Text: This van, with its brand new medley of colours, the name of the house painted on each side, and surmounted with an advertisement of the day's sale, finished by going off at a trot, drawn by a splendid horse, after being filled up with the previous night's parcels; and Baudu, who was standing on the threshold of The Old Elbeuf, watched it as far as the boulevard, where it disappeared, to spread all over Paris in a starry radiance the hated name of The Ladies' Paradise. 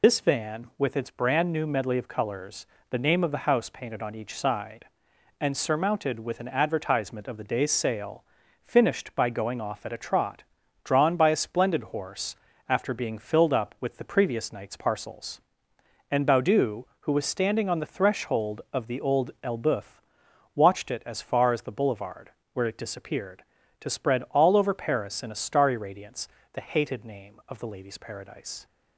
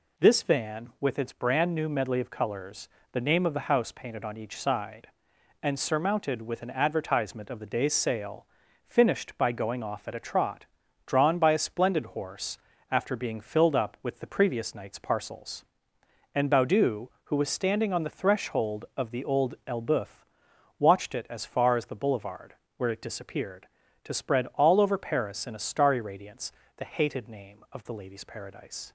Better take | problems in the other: second | loses the start of "This"; at 0.0 s; 75 ms // pauses between "radiance" and "the"; slight; at 26.2 s; 0.24 s long; slight in the second

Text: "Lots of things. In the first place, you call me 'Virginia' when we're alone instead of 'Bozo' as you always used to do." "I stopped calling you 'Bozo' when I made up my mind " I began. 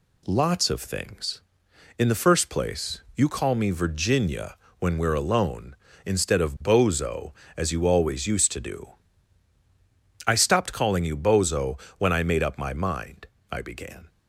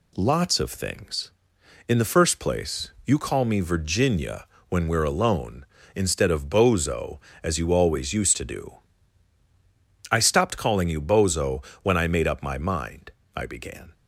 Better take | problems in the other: neither | pauses between "Virginia" and "when"; slight; the same in both // pauses between "Bozo" and "when"; slight; the same in both

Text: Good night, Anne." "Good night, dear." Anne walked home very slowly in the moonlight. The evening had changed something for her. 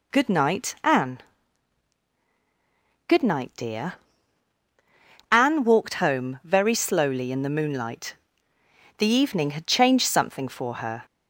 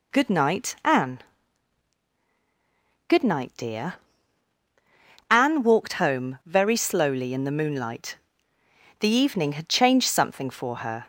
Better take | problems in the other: neither | none

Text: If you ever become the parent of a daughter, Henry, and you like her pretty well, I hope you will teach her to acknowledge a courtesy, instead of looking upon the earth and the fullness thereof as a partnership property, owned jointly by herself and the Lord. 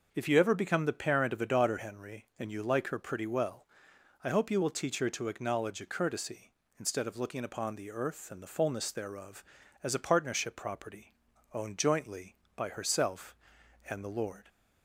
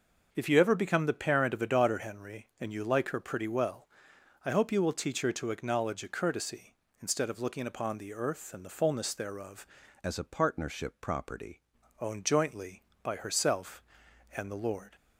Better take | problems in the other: first | changes voice from "as" to "property"; from 10.0 to 11.6 s; 1.6 s long

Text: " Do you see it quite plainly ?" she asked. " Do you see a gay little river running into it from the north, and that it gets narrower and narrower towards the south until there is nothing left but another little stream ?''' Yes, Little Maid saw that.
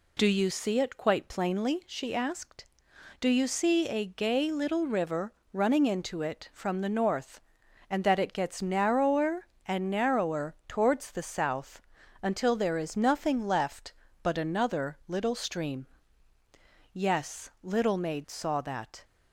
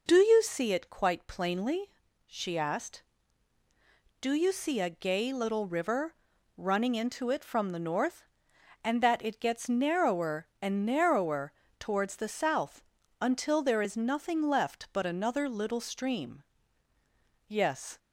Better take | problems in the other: first | pauses between "river" and "running"; at 6.1 s; 0.40 s long; slight in the first // pauses between "narrower" and "towards"; slight; at 11.5 s; 0.28 s long // pauses between "south" and "until"; slight; at 12.8 s; 0.36 s long; also in the first // stops before "Little Maid saw that"; at 17.9 s

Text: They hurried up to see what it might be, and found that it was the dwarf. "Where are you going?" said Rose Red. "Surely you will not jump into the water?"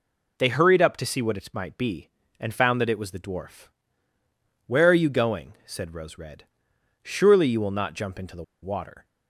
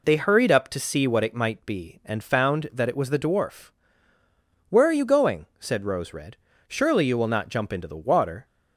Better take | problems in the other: second | pauses between "the" and "water"; slight; at 8.4 s; 0.19 s long

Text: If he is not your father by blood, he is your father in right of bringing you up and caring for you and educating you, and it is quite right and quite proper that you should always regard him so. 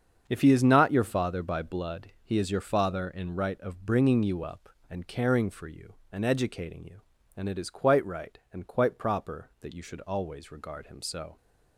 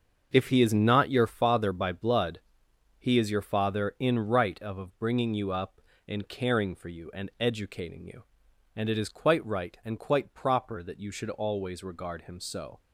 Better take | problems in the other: first | starts louder than the rest; until 1.3 s; 7 dB; also in the first // says "of" twice; at 4.7 s

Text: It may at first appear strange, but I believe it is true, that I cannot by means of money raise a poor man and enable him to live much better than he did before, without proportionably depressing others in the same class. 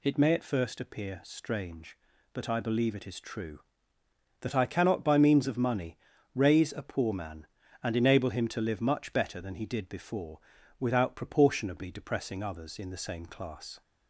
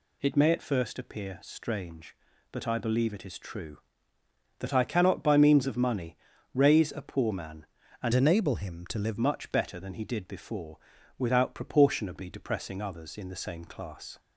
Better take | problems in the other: first | pauses between "money" and "raise"; slight; at 6.1 s; 0.36 s long; slight in the first // changes voice from "enable" to "live"; from 8.1 to 9.1 s; 1.0 s long

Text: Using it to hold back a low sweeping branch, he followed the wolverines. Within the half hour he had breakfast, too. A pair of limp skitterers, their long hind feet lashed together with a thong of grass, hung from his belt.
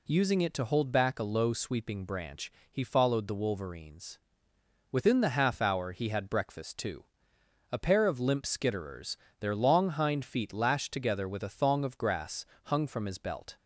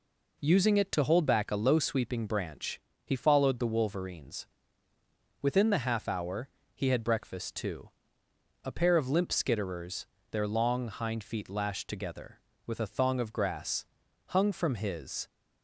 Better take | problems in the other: first | pauses between "hour" and "he"; slight; at 6.4 s; 0.26 s long // stops before "belt"; at 15.2 s

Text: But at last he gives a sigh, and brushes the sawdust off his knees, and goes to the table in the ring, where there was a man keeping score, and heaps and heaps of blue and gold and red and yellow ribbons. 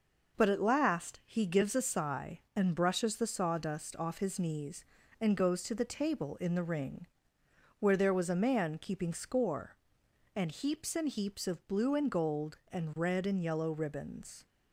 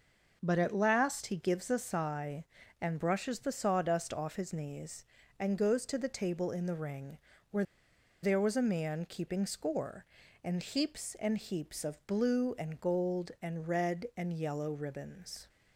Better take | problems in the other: first | pauses between "where" and "there"; noticeable; at 7.6 s; 0.57 s long

